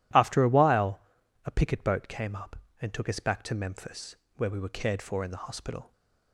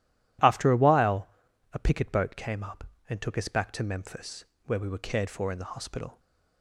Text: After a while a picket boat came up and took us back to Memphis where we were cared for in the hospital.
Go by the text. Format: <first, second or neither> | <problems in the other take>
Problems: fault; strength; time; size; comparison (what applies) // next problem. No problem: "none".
neither | pauses between "while" and "a"; noticeable; the same in both // pauses between "Memphis" and "where"; slight; the same in both